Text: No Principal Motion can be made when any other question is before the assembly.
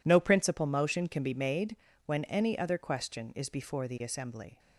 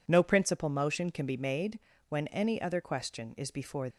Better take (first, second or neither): first